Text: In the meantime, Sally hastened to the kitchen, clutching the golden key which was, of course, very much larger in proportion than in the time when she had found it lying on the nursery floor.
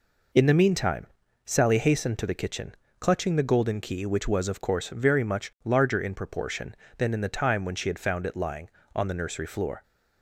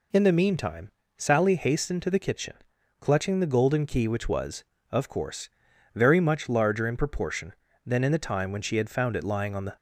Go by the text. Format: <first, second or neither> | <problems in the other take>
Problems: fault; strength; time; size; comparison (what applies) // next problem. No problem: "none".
first | stops before "nursery floor"; at 9.7 s